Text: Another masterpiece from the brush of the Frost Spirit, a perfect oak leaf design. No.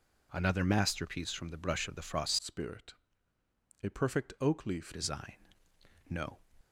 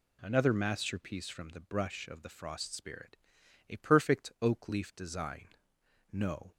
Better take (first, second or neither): second